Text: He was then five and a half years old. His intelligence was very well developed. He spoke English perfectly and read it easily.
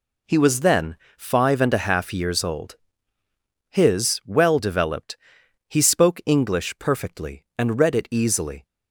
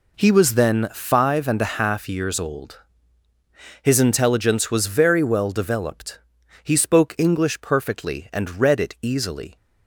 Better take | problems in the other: second | pauses between "then" and "five"; slight; at 0.9 s; 0.22 s long // skips "intelligence was very"; at 4.2 s

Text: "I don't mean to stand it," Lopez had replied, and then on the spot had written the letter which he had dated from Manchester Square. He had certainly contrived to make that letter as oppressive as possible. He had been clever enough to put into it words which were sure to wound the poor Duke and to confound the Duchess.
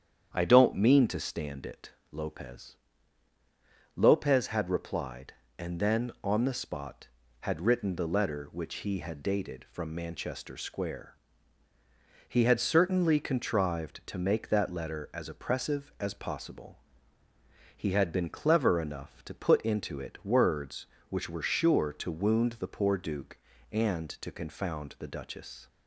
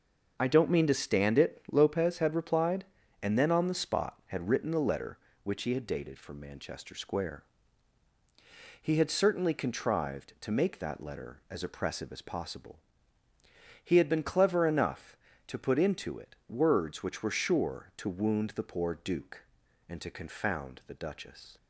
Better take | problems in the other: second | starts louder than the rest; strong; until 1.3 s; 8.5 dB // says "Lopez" twice; at 3.9 s

